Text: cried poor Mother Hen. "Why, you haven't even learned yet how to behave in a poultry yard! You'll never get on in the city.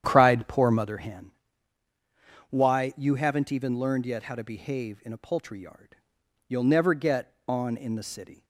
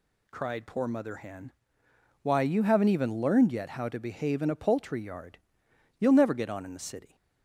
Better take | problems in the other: second | starts louder than the rest; strong; until 1.0 s; 9.5 dB

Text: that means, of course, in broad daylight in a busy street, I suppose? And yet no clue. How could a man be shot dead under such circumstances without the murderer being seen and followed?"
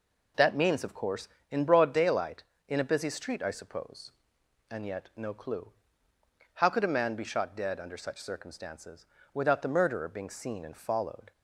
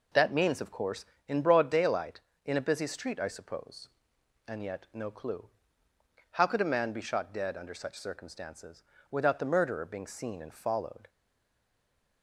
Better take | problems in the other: first | pauses between "circumstances" and "without"; slight; at 8.8 s; 0.28 s long; slight in the first // stays silent after the last word; from 11.0 s on; 1.2 s long

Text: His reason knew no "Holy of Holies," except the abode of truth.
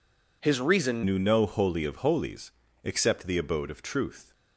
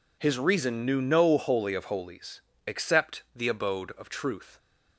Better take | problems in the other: second | changes voice at "knew"; from 1.0 s on; 3.3 s long

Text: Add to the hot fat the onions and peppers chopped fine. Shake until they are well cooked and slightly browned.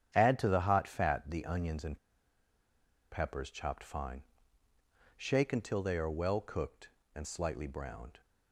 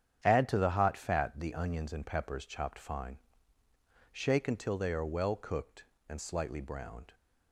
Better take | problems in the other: second | starts louder than the rest; strong; until 1.1 s; 9 dB; strong in the second // pauses between "and" and "peppers"; at 1.9 s; 1.1 s long

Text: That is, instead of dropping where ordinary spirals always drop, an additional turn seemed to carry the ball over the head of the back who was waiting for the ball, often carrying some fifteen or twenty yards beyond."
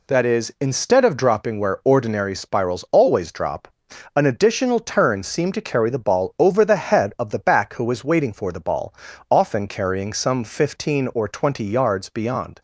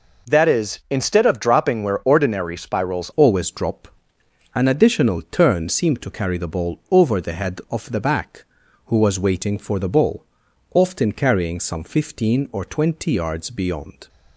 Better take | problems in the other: first | changes voice at "always"; from 3.1 s on; 10.9 s long

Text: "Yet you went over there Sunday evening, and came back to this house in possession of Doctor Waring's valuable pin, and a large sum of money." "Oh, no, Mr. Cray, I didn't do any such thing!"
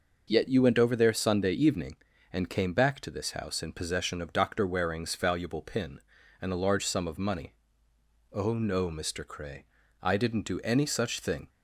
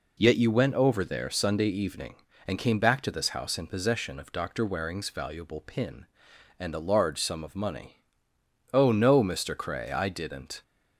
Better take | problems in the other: first | stops before "do any such thing"; at 10.6 s

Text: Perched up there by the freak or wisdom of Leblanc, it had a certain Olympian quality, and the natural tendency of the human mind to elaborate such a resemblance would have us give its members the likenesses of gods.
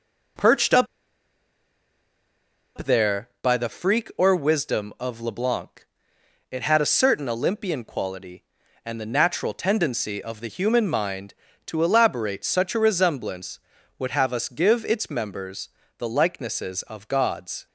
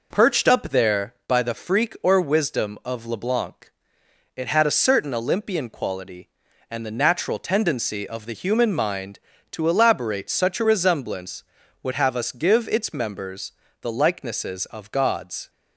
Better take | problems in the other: second | pauses between "up" and "there"; strong; at 0.8 s; 1.9 s long // pauses between "members" and "the"; slight; at 15.6 s; 0.30 s long; slight in the second

